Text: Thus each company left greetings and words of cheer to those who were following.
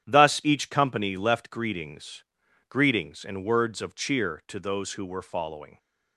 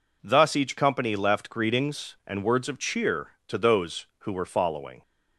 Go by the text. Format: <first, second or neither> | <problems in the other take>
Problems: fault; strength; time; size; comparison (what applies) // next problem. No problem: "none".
second | starts louder than the rest; strong; until 1.0 s; 9.5 dB // says "greetings" twice; at 2.6 s